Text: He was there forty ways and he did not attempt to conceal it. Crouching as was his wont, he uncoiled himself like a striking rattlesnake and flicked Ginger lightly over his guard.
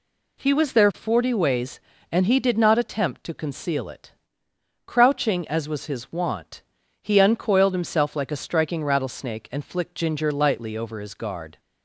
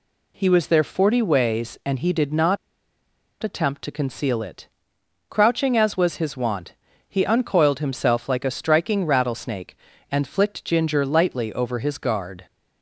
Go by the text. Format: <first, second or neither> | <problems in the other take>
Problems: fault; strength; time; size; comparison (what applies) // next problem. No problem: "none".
first | pauses between "not" and "attempt"; noticeable; at 2.5 s; 0.85 s long